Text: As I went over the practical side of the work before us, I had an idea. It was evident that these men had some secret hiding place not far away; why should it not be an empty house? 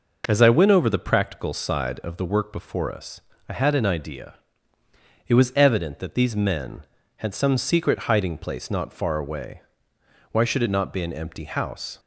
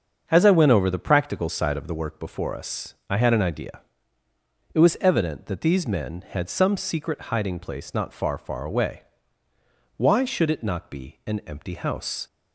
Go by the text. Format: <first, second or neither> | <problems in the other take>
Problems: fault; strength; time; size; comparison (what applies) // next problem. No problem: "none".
first | starts louder than the rest; until 1.2 s; 7 dB // says "far" twice; at 8.3 s